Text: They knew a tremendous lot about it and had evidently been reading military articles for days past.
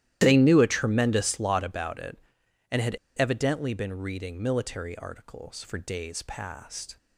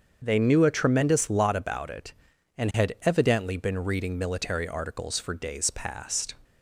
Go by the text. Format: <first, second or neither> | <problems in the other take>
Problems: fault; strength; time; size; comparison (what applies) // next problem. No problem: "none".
second | starts louder than the rest; strong; until 1.2 s; 13 dB; also in the second // pauses between "had" and "evidently"; slight; at 2.9 s; 0.22 s long